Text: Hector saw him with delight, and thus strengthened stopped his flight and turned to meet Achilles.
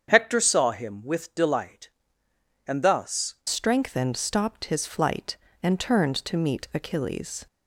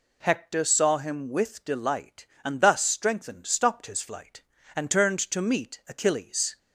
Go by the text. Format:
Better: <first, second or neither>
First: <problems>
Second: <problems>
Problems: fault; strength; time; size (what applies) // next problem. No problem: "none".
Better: second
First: starts louder than the rest; strong; until 1.1 s; 7.5 dB // changes voice at "strengthened"; from 3.4 s on; 4.0 s long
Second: none